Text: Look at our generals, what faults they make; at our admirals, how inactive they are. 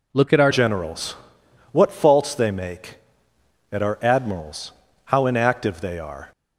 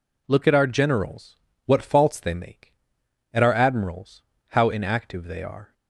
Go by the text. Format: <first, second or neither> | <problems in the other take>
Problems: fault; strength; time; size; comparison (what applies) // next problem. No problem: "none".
second | changes voice at "generals"; from 0.4 s on; 5.9 s long